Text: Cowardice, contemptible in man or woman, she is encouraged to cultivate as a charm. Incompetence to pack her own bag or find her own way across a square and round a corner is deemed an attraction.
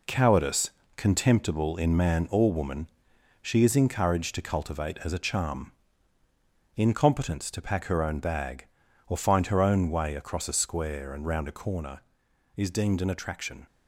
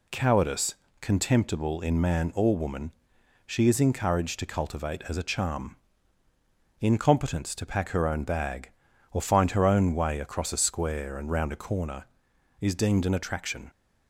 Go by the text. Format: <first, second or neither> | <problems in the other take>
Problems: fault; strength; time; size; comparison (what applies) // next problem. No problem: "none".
second | gets quieter; throughout; 7 dB